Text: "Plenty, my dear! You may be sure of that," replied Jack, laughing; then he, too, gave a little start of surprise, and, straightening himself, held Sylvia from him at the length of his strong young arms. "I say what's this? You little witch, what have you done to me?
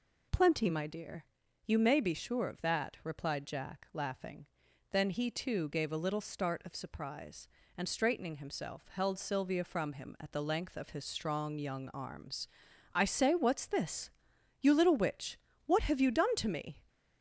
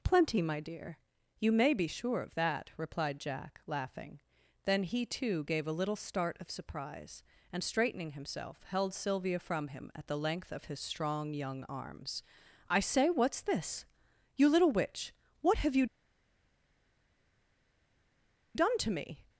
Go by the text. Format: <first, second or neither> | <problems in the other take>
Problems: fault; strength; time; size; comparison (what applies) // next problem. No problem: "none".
first | pauses between "you" and "done"; strong; at 15.8 s; 2.7 s long